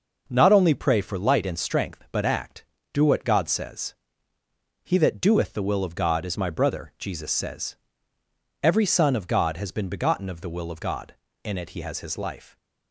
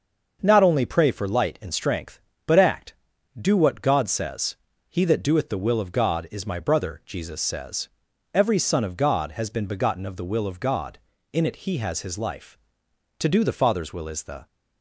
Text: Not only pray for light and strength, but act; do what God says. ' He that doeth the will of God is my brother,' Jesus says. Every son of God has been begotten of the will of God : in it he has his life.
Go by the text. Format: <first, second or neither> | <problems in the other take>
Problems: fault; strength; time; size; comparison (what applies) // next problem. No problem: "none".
first | starts louder than the rest; until 1.4 s; 6.5 dB // goes on to say "To do the Father's will is the"; noticeable; from 13.1 s on; 1.2 s long